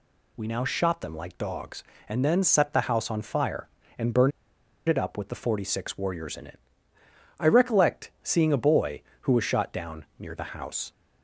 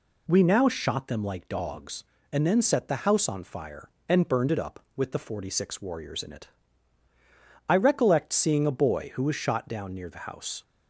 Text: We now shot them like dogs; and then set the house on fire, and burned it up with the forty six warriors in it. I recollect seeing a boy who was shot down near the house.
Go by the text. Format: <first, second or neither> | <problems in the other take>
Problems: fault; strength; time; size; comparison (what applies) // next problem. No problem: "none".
second | pauses between "burned" and "it"; noticeable; at 4.3 s; 0.57 s long